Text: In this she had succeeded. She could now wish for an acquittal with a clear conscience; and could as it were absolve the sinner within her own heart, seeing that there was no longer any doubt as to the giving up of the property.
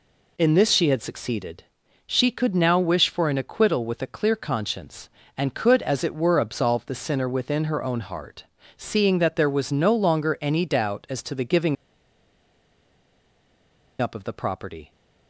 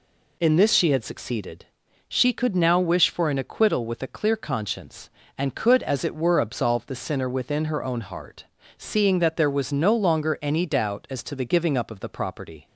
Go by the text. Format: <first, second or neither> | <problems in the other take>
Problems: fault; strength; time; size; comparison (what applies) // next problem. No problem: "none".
second | pauses between "giving" and "up"; strong; at 11.7 s; 2.2 s long